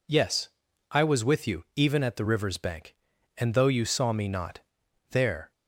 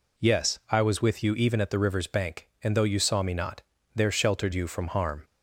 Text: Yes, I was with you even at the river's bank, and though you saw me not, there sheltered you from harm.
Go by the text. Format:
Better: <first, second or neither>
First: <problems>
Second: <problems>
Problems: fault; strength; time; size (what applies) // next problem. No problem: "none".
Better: second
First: stops before "sheltered you from harm"; at 5.5 s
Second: none